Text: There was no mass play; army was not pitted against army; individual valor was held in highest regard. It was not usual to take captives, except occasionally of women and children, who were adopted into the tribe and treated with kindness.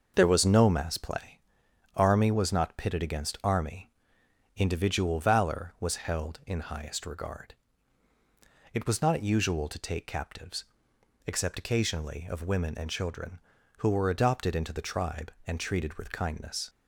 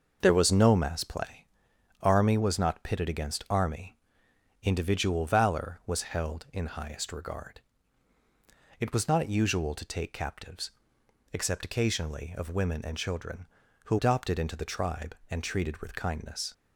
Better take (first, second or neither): first